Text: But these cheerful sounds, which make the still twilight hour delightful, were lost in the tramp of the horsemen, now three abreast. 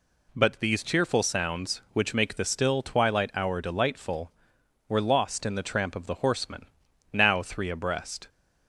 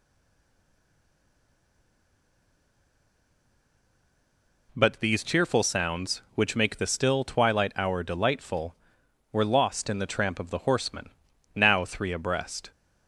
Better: first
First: none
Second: stays silent before the first word; strong; until 4.6 s; 4.6 s long

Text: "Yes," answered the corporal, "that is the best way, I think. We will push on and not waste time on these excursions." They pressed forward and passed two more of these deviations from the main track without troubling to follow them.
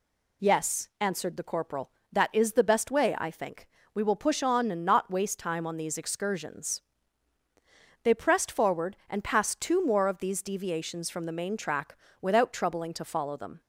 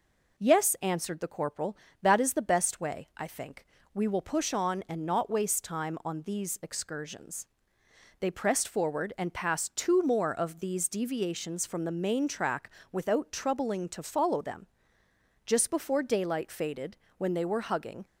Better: first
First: pauses between "track" and "without"; slight; at 11.9 s; 0.28 s long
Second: pauses between "track" and "without"; slight; at 12.7 s; 0.20 s long // goes on to say "Just before daylight faded when they were hugging"; strong; from 15.4 s on; 2.5 s long

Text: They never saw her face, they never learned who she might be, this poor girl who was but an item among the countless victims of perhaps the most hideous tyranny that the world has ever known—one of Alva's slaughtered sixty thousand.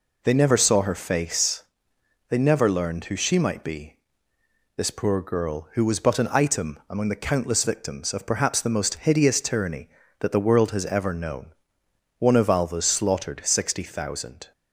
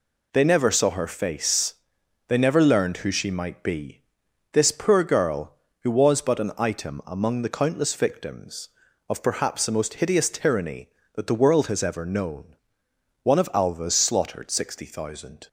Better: neither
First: none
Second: none

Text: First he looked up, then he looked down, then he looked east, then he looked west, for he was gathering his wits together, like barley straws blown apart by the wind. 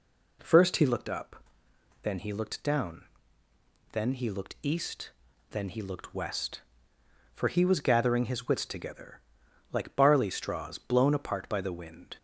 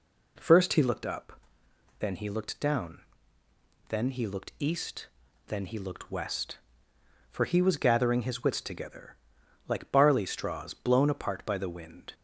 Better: neither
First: none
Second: none

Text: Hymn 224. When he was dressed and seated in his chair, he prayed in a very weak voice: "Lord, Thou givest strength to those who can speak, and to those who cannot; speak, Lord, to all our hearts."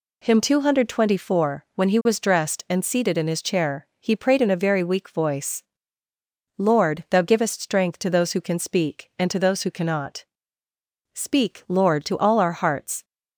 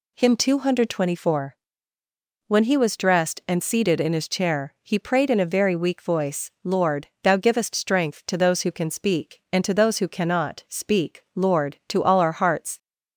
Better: neither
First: none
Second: none

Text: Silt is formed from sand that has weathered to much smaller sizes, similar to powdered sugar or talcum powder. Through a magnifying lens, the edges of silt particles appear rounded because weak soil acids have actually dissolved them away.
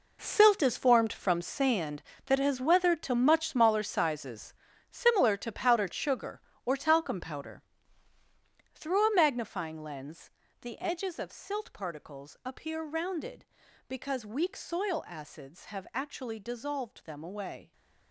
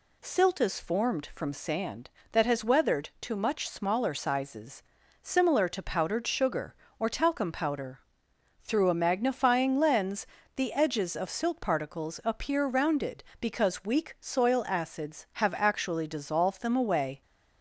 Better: second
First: gets quieter; strong; throughout; 12 dB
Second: none

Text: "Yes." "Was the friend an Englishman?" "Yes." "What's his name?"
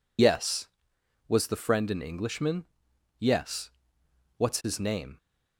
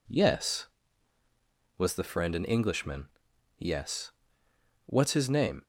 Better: second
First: loses the start of "Yes"; at 0.1 s; 60 ms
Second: none

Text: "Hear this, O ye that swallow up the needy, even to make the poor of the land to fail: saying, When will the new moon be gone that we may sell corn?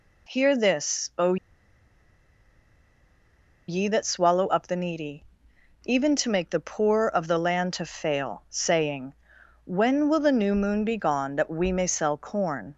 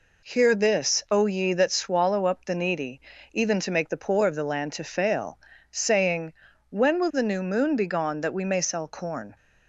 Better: second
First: pauses between "O" and "ye"; strong; at 1.3 s; 2.3 s long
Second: none

